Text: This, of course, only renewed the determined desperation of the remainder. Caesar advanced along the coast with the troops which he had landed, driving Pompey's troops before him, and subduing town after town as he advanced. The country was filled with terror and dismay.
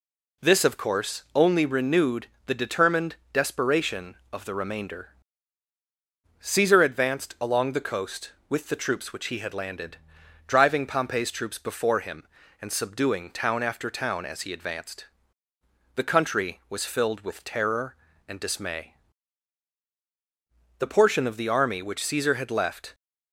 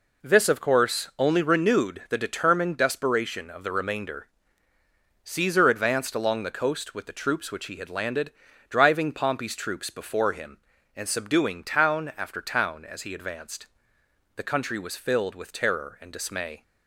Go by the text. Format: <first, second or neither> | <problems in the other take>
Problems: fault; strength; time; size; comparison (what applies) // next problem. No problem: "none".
second | pauses between "renewed" and "the"; slight; at 2.2 s; 0.20 s long // pauses between "determined" and "desperation"; slight; at 3.1 s; 0.16 s long // goes on to say "The portion of the army which Caesar had left"; strong; from 20.7 s on; 2.1 s long